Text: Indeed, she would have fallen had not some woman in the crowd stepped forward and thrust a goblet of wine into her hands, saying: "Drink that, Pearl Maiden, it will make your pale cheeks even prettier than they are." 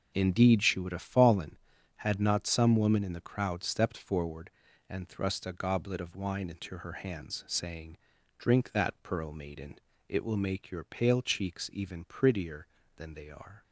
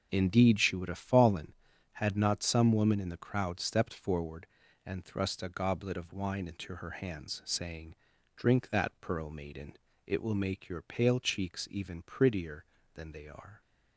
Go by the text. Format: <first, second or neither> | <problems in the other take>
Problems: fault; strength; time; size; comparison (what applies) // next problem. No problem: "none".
neither | none